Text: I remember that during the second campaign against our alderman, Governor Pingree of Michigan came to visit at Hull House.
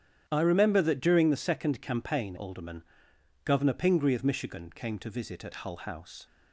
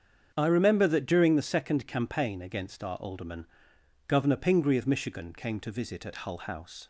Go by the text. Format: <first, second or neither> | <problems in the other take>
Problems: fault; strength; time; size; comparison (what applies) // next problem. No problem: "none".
second | starts louder than the rest; strong; until 1.2 s; 10 dB; strong in the second // skips "against our"; at 2.3 s